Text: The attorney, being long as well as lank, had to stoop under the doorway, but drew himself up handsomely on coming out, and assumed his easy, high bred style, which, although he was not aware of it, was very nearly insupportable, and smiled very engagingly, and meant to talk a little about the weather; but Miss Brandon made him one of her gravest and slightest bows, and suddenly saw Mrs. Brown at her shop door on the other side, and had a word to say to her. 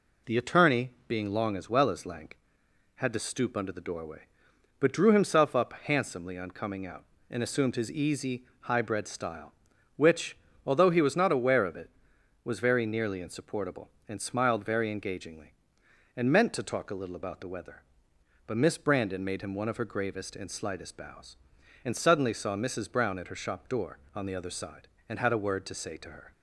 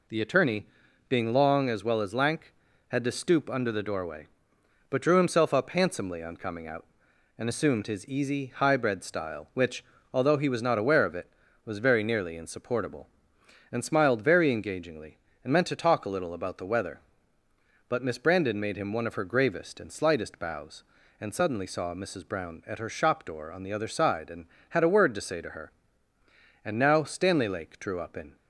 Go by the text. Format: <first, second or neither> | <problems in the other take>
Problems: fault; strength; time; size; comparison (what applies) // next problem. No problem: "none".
first | goes on to say "And now Stanley Lake drew up in"; strong; from 26.6 s on; 1.7 s long